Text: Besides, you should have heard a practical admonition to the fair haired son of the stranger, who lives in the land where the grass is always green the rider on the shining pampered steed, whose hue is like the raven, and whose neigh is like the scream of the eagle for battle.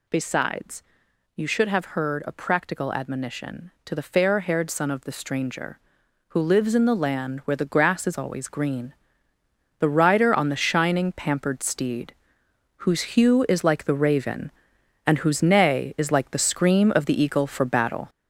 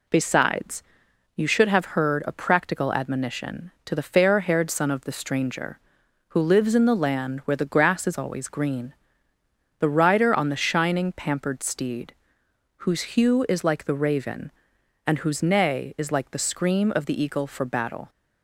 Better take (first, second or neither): second